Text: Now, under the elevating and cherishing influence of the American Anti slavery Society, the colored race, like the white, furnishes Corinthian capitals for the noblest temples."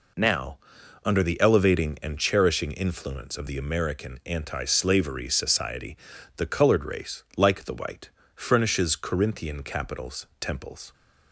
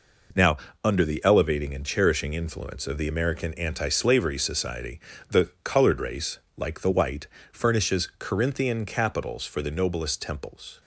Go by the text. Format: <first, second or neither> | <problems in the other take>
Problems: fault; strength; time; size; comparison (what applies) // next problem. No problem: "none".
second | skips "for the noblest"; at 10.3 s